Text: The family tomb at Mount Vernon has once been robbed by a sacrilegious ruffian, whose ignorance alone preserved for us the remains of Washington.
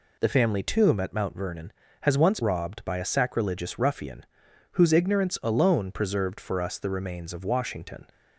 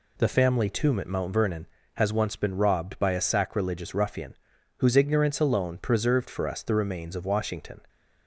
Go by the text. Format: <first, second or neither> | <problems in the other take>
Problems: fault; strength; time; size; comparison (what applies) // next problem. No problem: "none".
second | skips "been"; at 2.4 s